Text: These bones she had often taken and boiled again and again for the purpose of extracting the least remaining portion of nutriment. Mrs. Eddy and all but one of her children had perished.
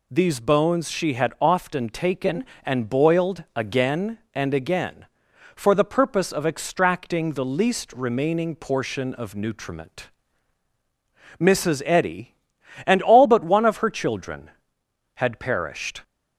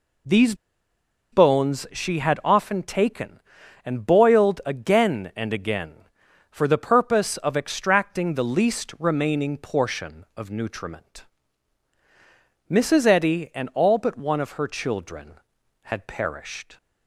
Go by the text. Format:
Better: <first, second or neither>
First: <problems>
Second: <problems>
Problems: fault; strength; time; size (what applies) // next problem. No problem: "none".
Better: first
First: none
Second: pauses between "These" and "bones"; noticeable; at 0.5 s; 0.76 s long